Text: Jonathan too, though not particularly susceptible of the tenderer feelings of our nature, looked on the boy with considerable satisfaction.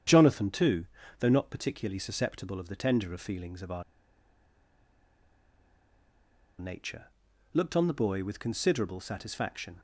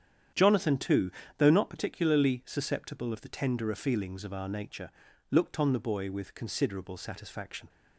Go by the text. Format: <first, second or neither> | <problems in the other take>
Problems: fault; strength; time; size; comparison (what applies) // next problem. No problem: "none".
second | starts louder than the rest; strong; until 1.3 s; 8.5 dB; strong in the second // pauses between "our" and "nature"; strong; at 3.8 s; 2.7 s long